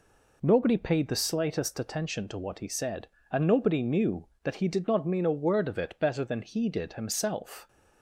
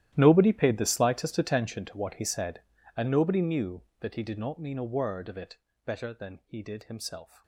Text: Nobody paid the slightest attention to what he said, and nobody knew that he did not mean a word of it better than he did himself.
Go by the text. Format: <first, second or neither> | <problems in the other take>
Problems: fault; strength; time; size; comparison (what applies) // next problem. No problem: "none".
first | gets quieter; strong; throughout; 18.5 dB // pauses between "it" and "better"; slight; at 5.5 s; 0.30 s long